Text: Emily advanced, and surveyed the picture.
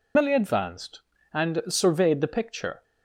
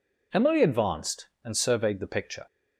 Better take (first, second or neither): second